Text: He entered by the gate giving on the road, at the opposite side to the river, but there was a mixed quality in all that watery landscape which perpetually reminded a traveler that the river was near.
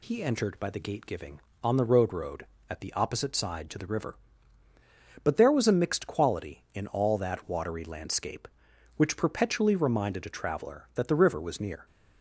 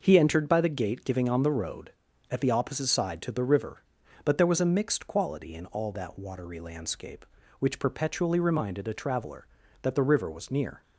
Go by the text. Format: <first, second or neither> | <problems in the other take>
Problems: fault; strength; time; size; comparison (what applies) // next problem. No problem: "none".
second | says "road" twice; at 2.1 s